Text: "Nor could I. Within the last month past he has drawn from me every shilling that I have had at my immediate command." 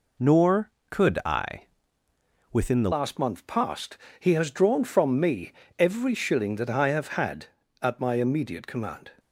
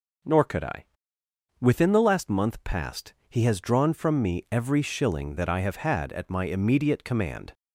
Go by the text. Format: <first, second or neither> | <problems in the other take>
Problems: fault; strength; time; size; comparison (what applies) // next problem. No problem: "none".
second | changes voice at "last"; from 2.9 s on; 6.2 s long // pauses between "past" and "he"; slight; at 3.9 s; 0.22 s long; slight in the second // pauses between "me" and "every"; slight; at 5.5 s; 0.26 s long